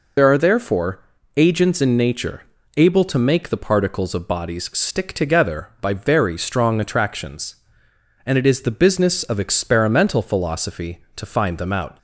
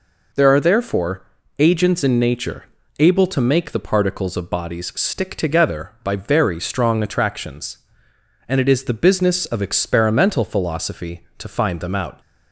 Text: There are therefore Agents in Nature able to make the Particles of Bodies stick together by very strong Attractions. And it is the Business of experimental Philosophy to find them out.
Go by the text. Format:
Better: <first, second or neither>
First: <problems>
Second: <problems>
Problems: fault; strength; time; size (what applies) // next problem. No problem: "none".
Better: second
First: loses the start of "There"; at 0.1 s; 55 ms // pauses between "therefore" and "Agents"; slight; at 1.0 s; 0.34 s long // pauses between "Nature" and "able"; slight; at 2.4 s; 0.34 s long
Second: pauses between "therefore" and "Agents"; slight; at 1.2 s; 0.34 s long // pauses between "Nature" and "able"; slight; at 2.6 s; 0.34 s long